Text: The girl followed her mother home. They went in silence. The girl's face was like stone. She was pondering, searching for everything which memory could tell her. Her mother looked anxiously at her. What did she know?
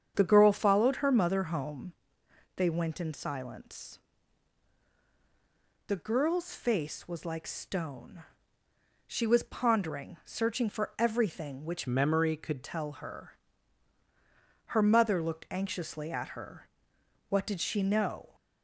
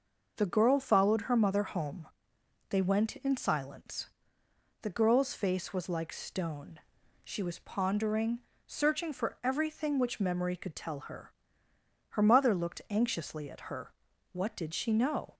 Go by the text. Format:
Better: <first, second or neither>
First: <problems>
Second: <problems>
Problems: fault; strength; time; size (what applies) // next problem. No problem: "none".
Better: second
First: starts louder than the rest; strong; until 1.1 s; 8 dB // changes voice from "memory" to "could"; from 11.8 to 12.6 s; 0.8 s long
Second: none